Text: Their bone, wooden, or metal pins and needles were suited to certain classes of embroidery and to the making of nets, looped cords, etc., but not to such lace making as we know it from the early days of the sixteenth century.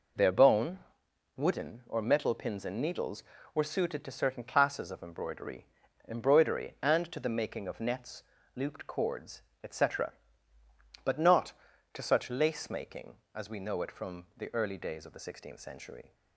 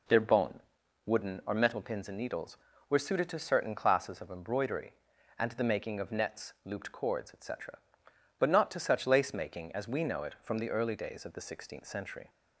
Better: second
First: says "embroidery" twice; at 6.0 s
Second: none

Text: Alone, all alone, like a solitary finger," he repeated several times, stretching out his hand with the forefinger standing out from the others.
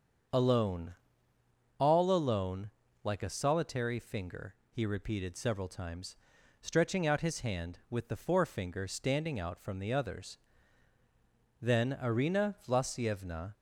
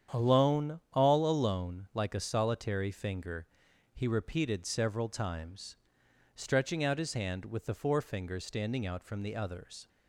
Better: second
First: starts louder than the rest; strong; until 2.2 s; 7 dB // goes on to say "Then Arina Vlasyevna"; strong; from 11.6 s on; 1.9 s long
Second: starts louder than the rest; strong; until 1.2 s; 8.5 dB

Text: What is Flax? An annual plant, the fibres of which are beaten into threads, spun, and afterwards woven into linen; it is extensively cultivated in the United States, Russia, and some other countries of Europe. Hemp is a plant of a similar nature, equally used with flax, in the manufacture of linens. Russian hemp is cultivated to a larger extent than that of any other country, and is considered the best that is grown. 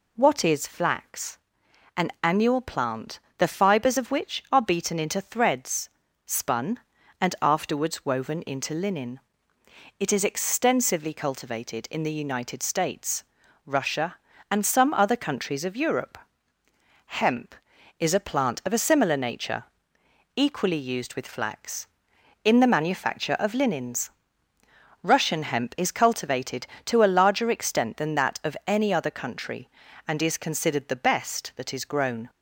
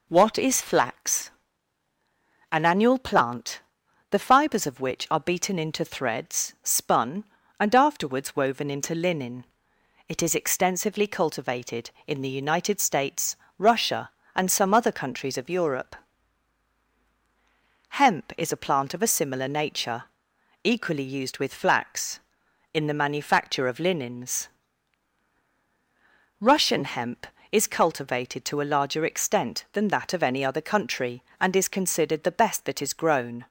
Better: neither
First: none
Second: none

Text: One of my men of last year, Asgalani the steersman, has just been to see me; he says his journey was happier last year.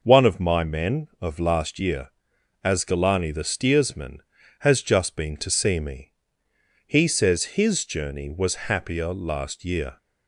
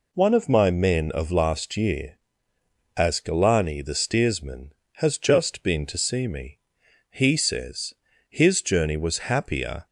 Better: first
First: none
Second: pauses between "says" and "his"; at 7.9 s; 0.38 s long // stops before "last year"; at 9.8 s

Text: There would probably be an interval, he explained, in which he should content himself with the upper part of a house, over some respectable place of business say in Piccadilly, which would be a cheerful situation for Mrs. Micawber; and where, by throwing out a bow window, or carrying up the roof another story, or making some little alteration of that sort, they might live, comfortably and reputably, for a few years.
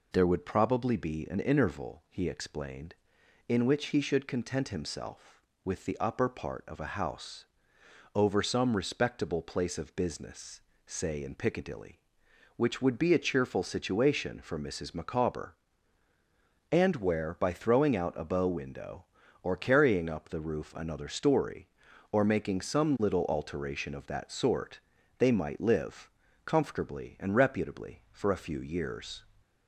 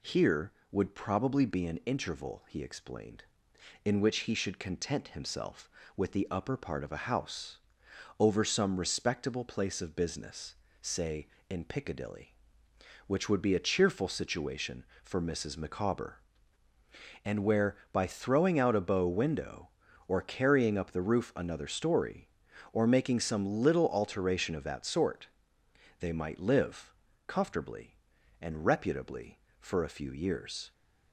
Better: first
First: pauses between "business" and "say"; slight; at 10.6 s; 0.24 s long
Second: says "Here" for "There"; at 0.0 s // pauses between "business" and "say"; slight; at 10.5 s; 0.28 s long

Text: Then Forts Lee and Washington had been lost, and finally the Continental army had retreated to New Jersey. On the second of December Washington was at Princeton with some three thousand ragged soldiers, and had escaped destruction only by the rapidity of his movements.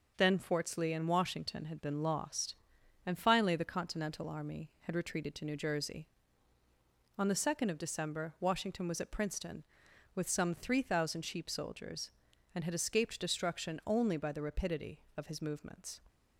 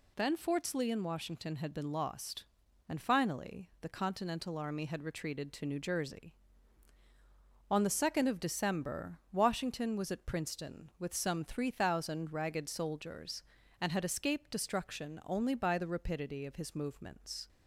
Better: second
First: says "sheep" for "ragged"; at 11.2 s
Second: none

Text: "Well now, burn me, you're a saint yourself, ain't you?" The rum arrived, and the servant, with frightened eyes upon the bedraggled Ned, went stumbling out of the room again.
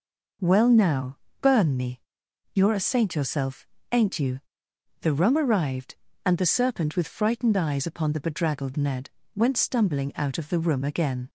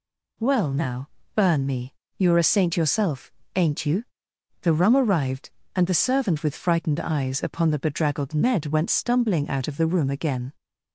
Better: second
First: says "serpent" for "servant"; at 6.4 s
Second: none

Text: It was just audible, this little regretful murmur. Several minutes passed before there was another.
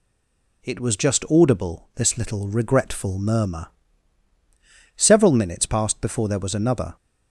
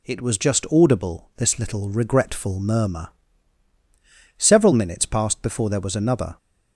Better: second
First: stays silent before the first word; slight; until 0.6 s; 0.6 s long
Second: none

